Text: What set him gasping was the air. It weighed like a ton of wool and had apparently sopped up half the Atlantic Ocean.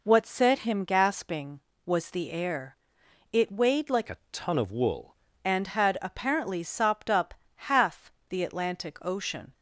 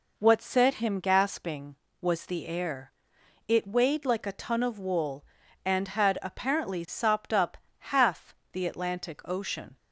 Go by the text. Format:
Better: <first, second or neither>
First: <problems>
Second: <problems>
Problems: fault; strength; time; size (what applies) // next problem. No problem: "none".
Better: second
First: changes voice from "a" to "wool"; from 4.0 to 5.1 s; 1.1 s long // pauses between "a" and "ton"; slight; at 4.1 s; 0.16 s long // pauses between "up" and "half"; slight; at 7.3 s; 0.22 s long // pauses between "half" and "the"; slight; at 8.1 s; 0.18 s long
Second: pauses between "up" and "half"; slight; at 7.5 s; 0.22 s long // pauses between "half" and "the"; slight; at 8.3 s; 0.18 s long